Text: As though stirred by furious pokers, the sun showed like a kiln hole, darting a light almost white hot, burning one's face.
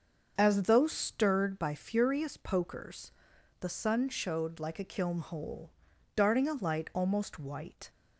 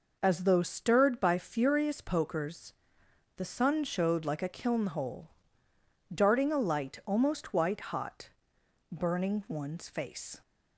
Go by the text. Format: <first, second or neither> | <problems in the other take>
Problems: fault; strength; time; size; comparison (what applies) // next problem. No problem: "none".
second | starts louder than the rest; until 1.3 s; 6.5 dB // stops before "hot burning one's face"; at 7.8 s